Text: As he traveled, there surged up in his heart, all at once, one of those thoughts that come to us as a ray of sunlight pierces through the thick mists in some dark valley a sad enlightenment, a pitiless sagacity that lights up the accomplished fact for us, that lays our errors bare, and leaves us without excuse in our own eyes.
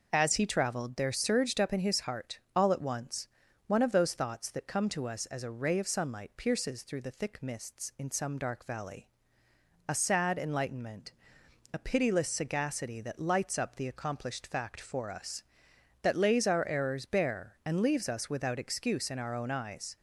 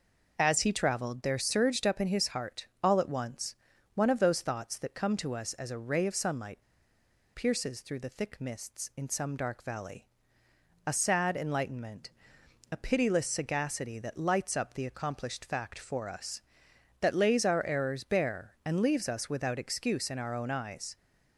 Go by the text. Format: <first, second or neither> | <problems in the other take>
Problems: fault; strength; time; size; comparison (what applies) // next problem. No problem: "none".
first | pauses between "sunlight" and "pierces"; noticeable; at 6.5 s; 0.75 s long // pauses between "valley" and "a"; noticeable; at 10.0 s; 0.80 s long; noticeable in the first